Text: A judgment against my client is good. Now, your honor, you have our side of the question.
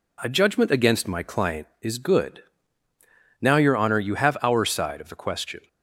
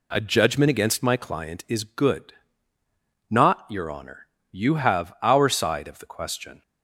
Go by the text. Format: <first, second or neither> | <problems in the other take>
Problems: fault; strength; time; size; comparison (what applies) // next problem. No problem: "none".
first | says "Not" for "Now"; at 3.2 s